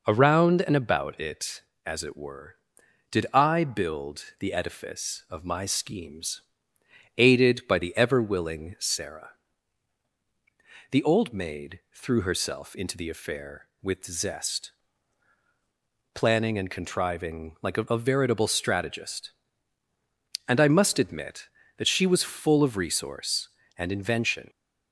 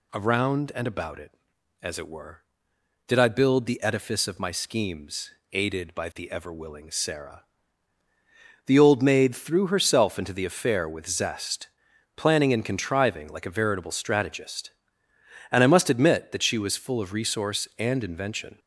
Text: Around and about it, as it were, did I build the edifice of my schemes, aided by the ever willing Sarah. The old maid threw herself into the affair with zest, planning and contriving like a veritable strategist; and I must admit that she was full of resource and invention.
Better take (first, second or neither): second